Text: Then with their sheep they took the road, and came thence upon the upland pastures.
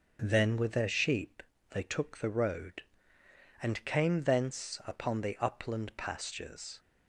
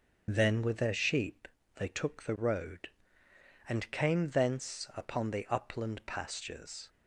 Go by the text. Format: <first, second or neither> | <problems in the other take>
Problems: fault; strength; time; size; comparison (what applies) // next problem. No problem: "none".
first | loses the start of "Then"; at 0.2 s; 35 ms // starts louder than the rest; until 1.2 s; 6.5 dB; also in the first // pauses between "sheep" and "they"; slight; at 1.4 s; 0.28 s long; slight in the first